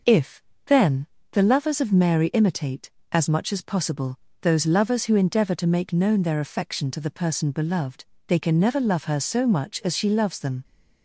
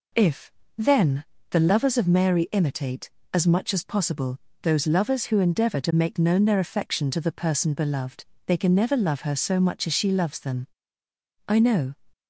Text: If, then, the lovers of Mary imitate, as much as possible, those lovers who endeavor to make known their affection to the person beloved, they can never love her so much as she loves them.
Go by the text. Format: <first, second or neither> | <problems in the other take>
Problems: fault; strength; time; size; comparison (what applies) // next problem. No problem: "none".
first | goes on to say "I know"; slight; from 11.4 s on; 0.46 s long